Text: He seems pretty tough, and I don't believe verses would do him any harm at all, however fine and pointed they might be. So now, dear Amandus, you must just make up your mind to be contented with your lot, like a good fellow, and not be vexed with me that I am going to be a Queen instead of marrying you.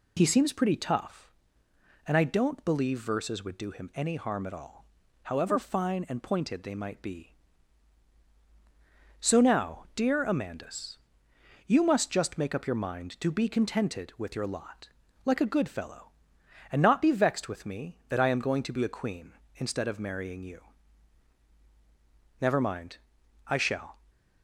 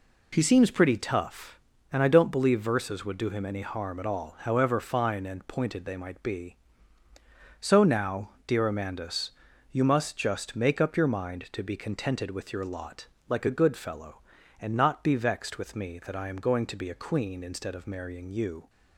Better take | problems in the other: second | goes on to say "Never mind I shall"; from 22.3 s on; 1.5 s long

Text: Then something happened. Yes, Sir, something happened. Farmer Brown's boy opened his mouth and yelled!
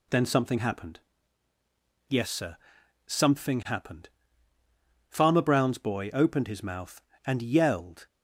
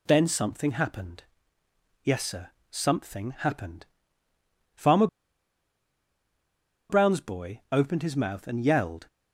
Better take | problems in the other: first | pauses between "Farmer" and "Brown's"; strong; at 5.0 s; 1.8 s long

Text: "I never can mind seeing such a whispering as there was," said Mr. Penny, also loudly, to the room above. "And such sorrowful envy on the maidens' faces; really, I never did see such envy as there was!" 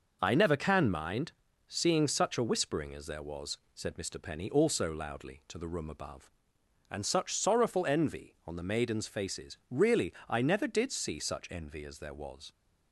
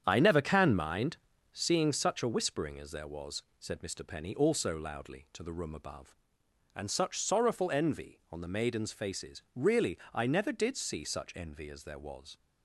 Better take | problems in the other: first | starts louder than the rest; strong; until 1.8 s; 8.5 dB // pauses between "mind" and "seeing"; at 1.1 s; 0.38 s long; also in the first

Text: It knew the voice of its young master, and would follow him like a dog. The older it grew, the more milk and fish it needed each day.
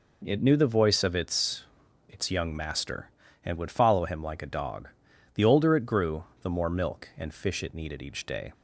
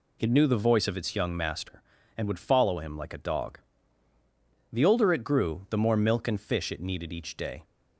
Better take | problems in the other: second | says "its" twice; at 2.0 s

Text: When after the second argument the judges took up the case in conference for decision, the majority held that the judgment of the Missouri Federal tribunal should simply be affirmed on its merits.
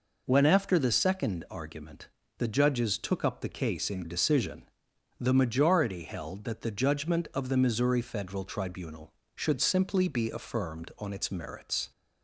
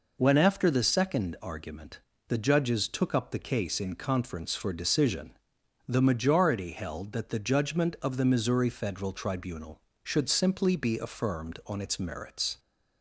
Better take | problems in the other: second | pauses between "argument" and "the"; slight; at 2.0 s; 0.32 s long; slight in the second // skips "conference for"; at 4.0 s

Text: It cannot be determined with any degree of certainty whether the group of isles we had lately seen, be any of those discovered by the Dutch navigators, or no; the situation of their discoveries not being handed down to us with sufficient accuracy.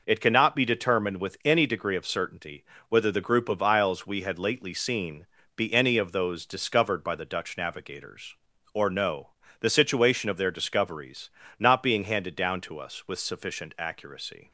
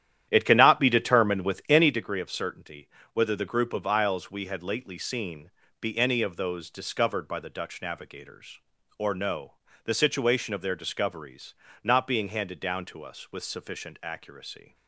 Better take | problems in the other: first | starts louder than the rest; strong; until 2.1 s; 11 dB // pauses between "certainty" and "whether"; slight; at 2.8 s; 0.24 s long; slight in the first // pauses between "discoveries" and "not"; slight; at 11.5 s; 0.30 s long; slight in the first

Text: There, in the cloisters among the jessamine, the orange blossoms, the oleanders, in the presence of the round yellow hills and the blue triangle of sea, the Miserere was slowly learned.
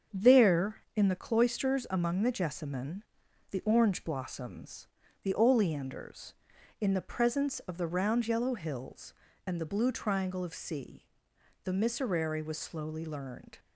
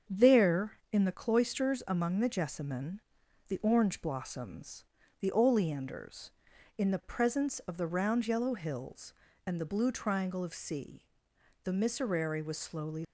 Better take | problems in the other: first | starts louder than the rest; strong; until 1.2 s; 7.5 dB; strong in the first // stops before "learned"; at 13.0 s

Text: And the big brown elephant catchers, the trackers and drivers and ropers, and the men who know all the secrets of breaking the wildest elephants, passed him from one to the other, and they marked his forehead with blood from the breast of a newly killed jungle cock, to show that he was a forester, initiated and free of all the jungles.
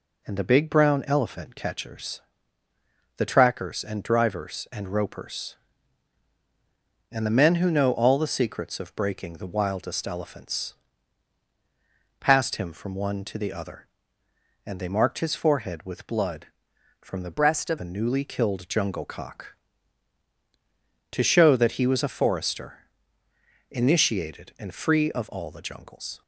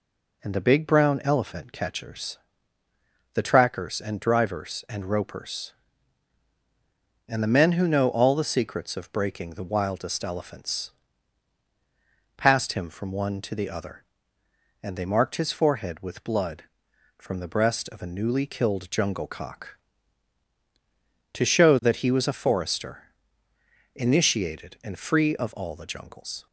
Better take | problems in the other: second | changes voice from "breast" to "of"; from 17.3 to 17.7 s; 0.4 s long

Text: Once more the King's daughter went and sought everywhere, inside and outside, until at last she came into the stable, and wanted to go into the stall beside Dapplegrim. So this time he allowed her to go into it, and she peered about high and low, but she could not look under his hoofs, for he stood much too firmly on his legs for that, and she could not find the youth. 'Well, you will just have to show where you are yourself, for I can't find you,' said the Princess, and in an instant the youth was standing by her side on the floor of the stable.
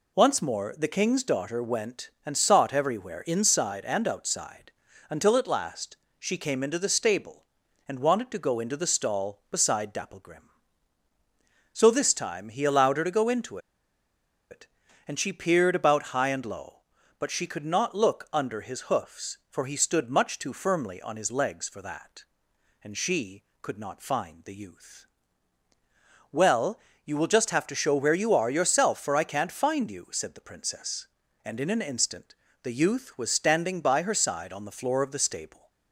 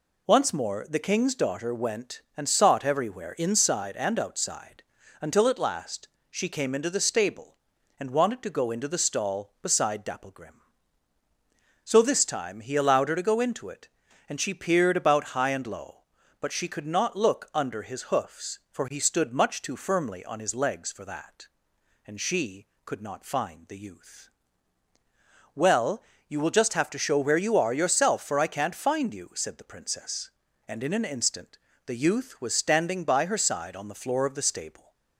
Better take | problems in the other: second | pauses between "last" and "she"; slight; at 5.9 s; 0.24 s long; slight in the second // pauses between "into" and "it"; noticeable; at 13.5 s; 0.92 s long // pauses between "instant" and "the"; slight; at 32.3 s; 0.28 s long; slight in the second

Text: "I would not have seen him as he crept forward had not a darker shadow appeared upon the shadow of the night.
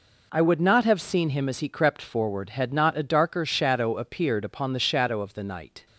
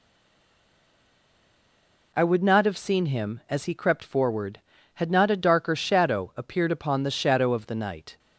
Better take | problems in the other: first | stays silent before the first word; until 2.1 s; 2.1 s long

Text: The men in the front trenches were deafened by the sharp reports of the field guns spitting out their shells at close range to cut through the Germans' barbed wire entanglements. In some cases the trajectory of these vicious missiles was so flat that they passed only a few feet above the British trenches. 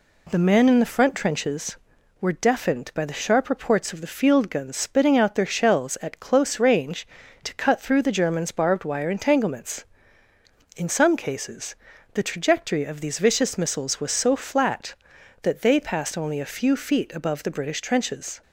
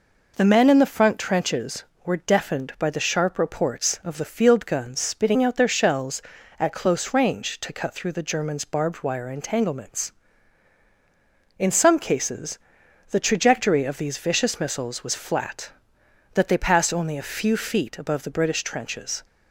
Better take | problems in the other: first | pauses between "cases" and "the"; noticeable; at 12.5 s; 0.50 s long; slight in the first // skips "so"; at 15.1 s

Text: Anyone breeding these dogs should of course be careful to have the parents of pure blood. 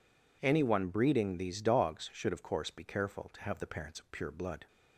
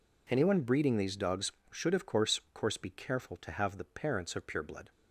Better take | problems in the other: first | says "course" twice; at 2.5 s

